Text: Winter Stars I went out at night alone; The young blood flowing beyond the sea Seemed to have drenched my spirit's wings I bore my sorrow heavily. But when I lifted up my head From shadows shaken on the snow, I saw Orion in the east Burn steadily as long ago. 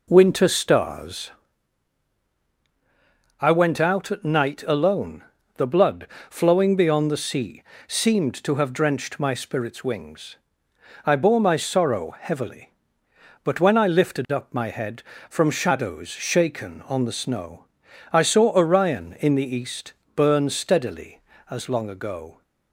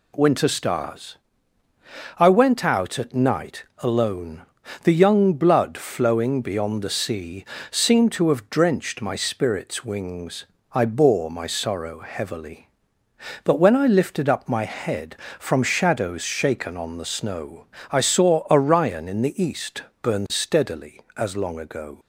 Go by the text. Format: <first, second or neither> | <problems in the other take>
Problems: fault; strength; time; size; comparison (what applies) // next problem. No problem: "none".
second | pauses between "Stars" and "I"; strong; at 1.3 s; 2.1 s long; also in the second // skips "young"; at 5.6 s // pauses between "blood" and "flowing"; slight; at 6.0 s; 0.22 s long // pauses between "sea" and "Seemed"; slight; at 7.6 s; 0.26 s long; slight in the second // pauses between "wings" and "I"; noticeable; at 10.3 s; 0.68 s long; slight in the second // pauses between "east" and "Burn"; slight; at 19.9 s; 0.20 s long; slight in the second